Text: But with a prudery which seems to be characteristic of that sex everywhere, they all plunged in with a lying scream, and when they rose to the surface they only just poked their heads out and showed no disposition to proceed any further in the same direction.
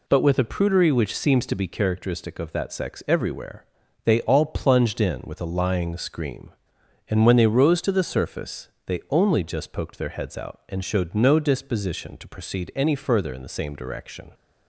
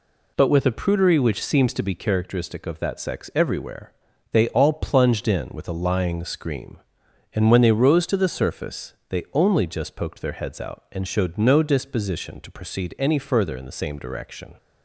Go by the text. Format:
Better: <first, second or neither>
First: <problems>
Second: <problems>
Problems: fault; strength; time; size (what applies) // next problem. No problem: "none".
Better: neither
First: pauses between "surface" and "they"; slight; at 8.6 s; 0.18 s long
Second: pauses between "surface" and "they"; slight; at 8.9 s; 0.16 s long